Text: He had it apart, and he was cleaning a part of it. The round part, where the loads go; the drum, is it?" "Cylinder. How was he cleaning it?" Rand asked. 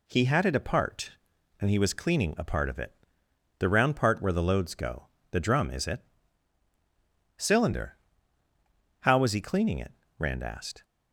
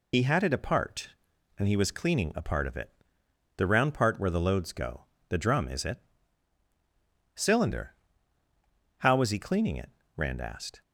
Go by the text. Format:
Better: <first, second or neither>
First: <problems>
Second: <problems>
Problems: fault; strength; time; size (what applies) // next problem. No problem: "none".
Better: first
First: none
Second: loses the start of "He"; at 0.1 s; 80 ms